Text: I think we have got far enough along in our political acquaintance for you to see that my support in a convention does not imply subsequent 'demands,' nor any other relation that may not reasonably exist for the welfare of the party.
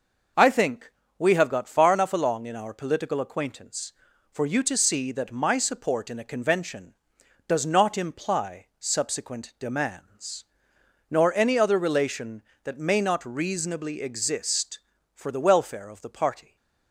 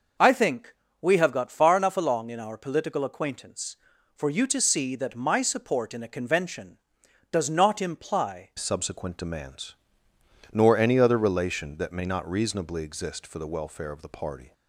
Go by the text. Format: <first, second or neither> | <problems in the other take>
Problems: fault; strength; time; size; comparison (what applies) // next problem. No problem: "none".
first | pauses between "think" and "we"; slight; at 0.7 s; 0.26 s long; slight in the first // changes voice at "subsequent"; from 8.5 s on; 6.0 s long